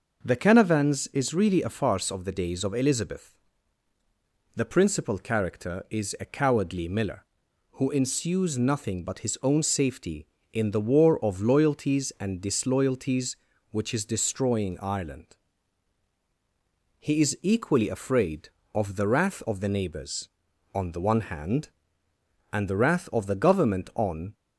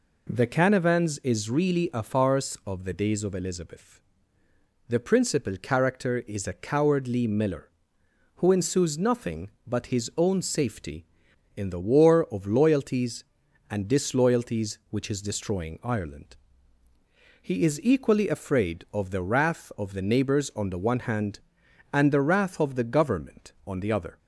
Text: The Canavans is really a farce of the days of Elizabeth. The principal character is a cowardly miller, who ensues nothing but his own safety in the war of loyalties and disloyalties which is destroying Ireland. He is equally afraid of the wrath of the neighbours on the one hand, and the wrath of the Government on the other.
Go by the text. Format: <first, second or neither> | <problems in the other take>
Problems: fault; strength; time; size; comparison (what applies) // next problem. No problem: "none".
second | stops before "the other"; at 24.3 s